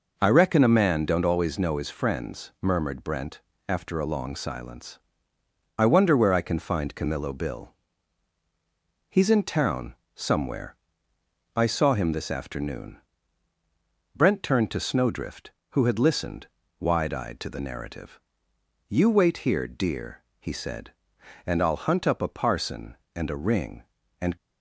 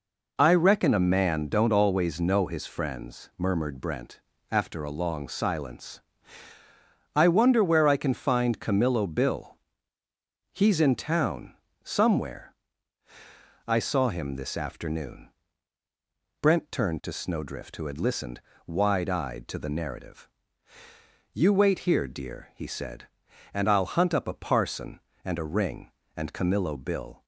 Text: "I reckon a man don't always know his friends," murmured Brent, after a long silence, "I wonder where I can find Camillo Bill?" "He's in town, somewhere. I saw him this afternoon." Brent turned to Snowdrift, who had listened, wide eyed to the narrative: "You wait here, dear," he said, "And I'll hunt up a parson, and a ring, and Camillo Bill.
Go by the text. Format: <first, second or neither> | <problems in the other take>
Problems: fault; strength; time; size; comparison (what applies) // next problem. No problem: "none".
second | stops before "Camillo Bill"; at 24.3 s